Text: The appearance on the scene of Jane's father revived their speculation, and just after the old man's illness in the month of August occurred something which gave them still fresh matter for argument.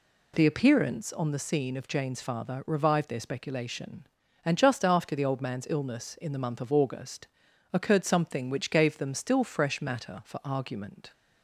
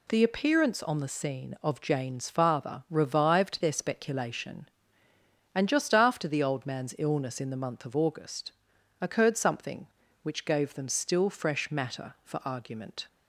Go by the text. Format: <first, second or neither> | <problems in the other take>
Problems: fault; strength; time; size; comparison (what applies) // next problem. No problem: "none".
neither | pauses between "August" and "occurred"; the same in both